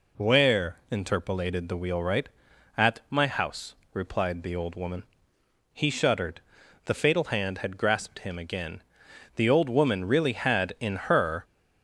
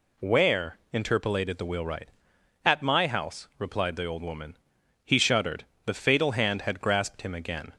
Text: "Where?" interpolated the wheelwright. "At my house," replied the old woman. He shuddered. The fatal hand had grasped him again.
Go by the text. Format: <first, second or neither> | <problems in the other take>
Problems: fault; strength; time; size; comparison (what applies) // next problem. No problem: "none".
second | goes on to say "The old woman really had in her"; strong; from 9.3 s on; 2.0 s long